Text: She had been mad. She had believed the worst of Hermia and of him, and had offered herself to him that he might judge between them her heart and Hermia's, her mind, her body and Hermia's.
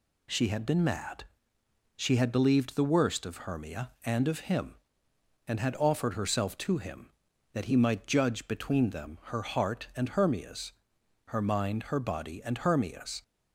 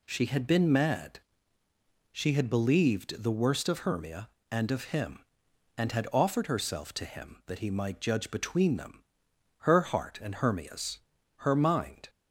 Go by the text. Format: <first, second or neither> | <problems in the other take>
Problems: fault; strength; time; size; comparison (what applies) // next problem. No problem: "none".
first | pauses between "them" and "her"; noticeable; at 9.0 s; 0.56 s long // stops before "her body and Hermia's"; at 12.0 s